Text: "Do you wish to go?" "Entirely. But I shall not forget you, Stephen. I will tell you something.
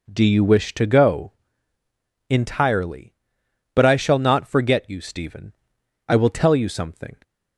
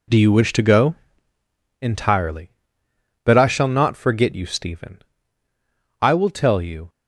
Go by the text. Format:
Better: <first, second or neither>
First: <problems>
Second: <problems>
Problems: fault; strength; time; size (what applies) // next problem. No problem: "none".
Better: first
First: none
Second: stops before "something"; at 6.8 s